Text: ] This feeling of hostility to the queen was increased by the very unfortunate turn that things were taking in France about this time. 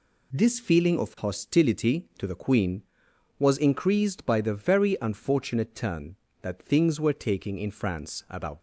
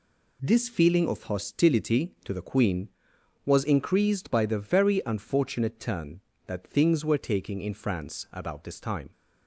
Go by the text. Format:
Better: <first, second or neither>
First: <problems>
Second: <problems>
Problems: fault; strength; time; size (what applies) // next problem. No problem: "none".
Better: second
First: stops before "this time"; at 8.5 s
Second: none